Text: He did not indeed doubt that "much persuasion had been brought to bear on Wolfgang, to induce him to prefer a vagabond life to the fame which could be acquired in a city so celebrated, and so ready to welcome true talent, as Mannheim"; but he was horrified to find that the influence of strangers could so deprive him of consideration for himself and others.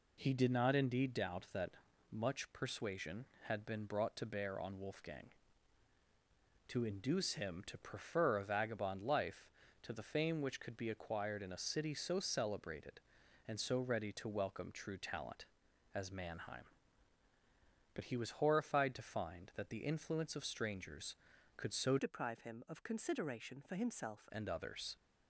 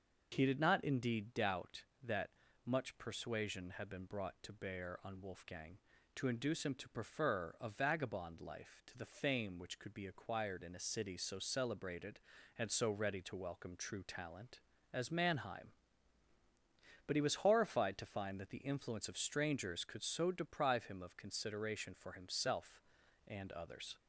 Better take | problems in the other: second | pauses between "that" and "much"; slight; at 1.7 s; 0.36 s long; slight in the second // changes voice from "deprive" to "himself"; from 21.9 to 24.2 s; 2.3 s long

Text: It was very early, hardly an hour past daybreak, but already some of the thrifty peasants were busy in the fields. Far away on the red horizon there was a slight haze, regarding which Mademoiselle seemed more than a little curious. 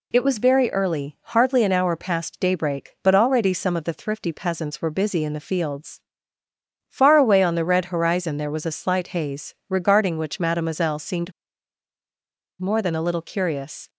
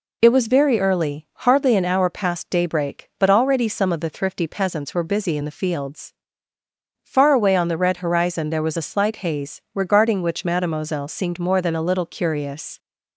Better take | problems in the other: second | pauses between "seemed" and "more"; strong; at 11.3 s; 1.2 s long

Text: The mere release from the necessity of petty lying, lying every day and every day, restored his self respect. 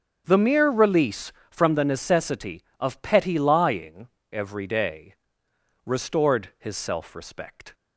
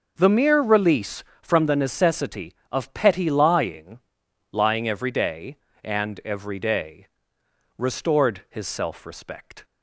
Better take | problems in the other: second | starts louder than the rest; until 1.2 s; 7 dB // skips "lying every day and"; at 4.1 s

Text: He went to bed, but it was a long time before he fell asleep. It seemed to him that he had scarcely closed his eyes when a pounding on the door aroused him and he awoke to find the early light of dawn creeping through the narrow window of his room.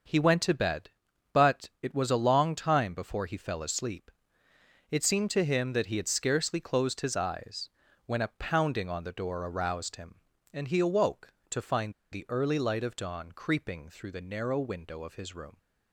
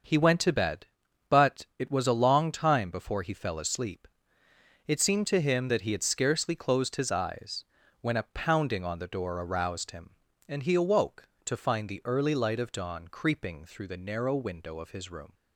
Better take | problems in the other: second | starts louder than the rest; until 1.5 s; 6.5 dB; also in the second // pauses between "eyes" and "when"; slight; at 7.6 s; 0.36 s long; slight in the second // pauses between "find" and "the"; slight; at 11.9 s; 0.19 s long

